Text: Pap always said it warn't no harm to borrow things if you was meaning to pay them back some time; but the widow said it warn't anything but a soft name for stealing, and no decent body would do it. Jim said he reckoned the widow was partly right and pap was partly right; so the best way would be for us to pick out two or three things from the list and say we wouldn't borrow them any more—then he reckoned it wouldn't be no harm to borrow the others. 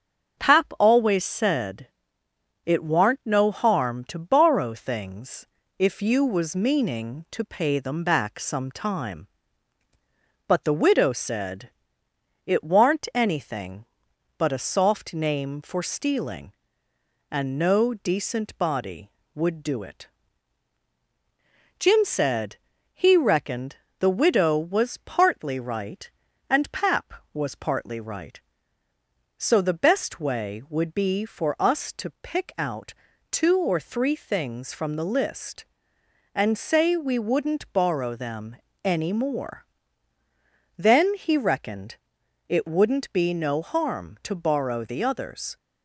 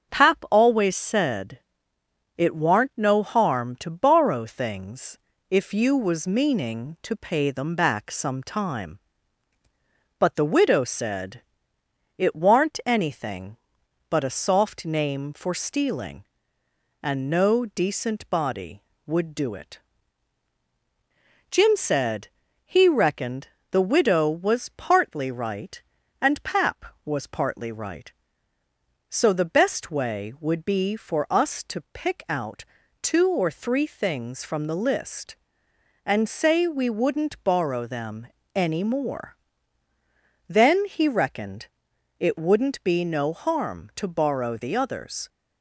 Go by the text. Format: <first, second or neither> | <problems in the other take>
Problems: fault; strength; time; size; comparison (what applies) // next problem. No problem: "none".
neither | starts louder than the rest; the same in both // pauses between "said" and "it"; noticeable; the same in both // pauses between "things" and "if"; slight; the same in both // pauses between "said" and "it"; noticeable; the same in both // pauses between "said" and "he"; slight; the same in both // pauses between "reckoned" and "the"; slight; the same in both // pauses between "out" and "two"; slight; the same in both // pauses between "them" and "any"; slight; the same in both // pauses between "reckoned" and "it"; noticeable; the same in both